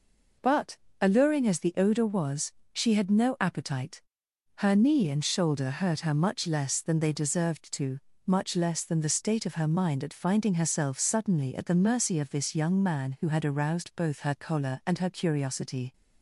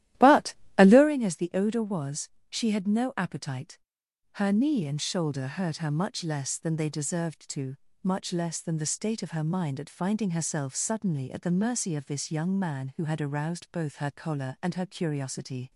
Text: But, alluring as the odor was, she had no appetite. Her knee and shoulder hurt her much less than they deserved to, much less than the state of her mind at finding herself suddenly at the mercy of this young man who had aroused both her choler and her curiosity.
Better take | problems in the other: first | starts louder than the rest; strong; until 1.1 s; 13.5 dB

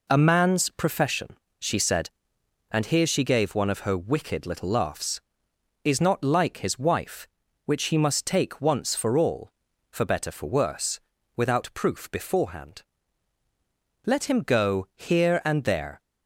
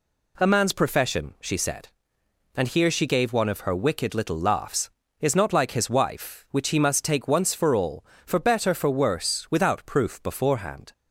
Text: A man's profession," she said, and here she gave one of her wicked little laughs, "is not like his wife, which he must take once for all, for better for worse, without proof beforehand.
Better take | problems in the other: second | goes on to say "Let him go here and there"; strong; from 14.0 s on; 1.9 s long

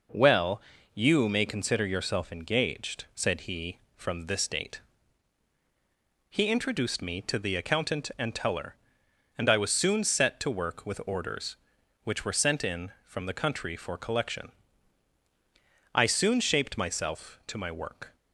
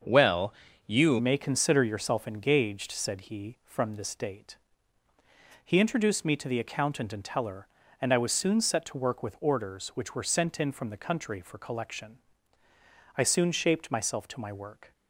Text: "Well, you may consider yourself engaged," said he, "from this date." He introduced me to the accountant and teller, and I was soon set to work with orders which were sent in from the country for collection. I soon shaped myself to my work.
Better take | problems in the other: first | starts louder than the rest; until 1.3 s; 6.5 dB // changes voice at "may"; from 1.1 s on; 13.8 s long

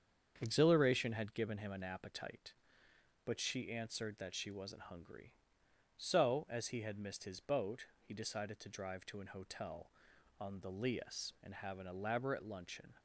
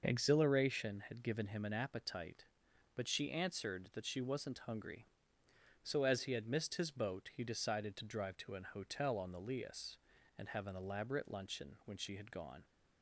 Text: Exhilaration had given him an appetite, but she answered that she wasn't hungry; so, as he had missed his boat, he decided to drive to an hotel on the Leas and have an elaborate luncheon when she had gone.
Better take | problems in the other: second | starts louder than the rest; strong; until 1.4 s; 7.5 dB // stops before "when she had gone"; at 12.9 s

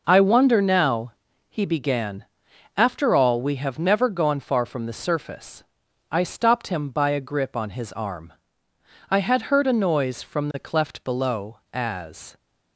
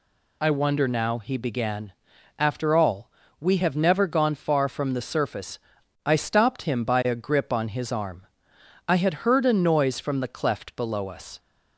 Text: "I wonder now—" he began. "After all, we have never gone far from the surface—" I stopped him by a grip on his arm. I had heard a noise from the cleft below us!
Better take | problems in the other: second | says "as" for "us"; at 11.7 s

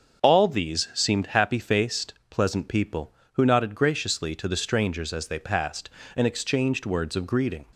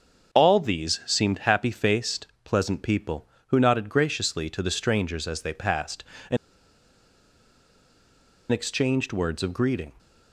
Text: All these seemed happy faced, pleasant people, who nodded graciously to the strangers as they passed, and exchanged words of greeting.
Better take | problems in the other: first | starts louder than the rest; until 1.3 s; 7 dB; also in the first // pauses between "and" and "exchanged"; strong; at 6.3 s; 2.1 s long

